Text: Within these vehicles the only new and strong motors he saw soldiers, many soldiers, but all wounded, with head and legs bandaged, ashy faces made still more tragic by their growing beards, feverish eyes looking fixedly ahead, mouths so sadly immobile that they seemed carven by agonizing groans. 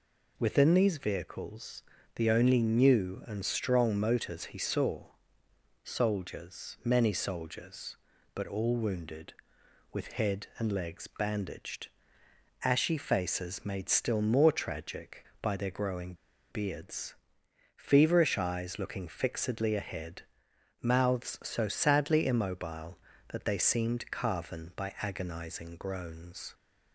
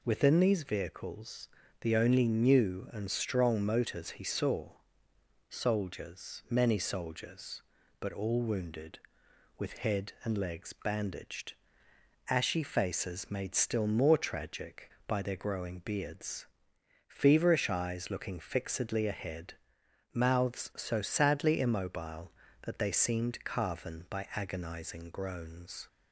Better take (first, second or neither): second